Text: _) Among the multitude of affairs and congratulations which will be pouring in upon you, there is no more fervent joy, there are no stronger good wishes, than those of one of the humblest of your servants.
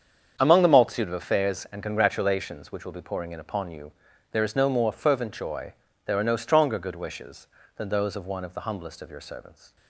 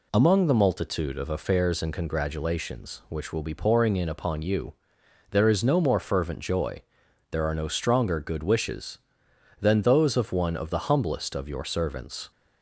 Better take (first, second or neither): second